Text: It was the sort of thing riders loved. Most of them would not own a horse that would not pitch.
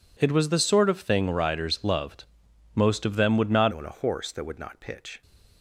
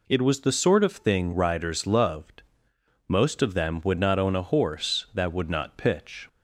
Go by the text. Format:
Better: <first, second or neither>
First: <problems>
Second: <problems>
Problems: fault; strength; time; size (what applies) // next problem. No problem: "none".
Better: second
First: changes voice at "own"; from 3.7 s on; 1.5 s long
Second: none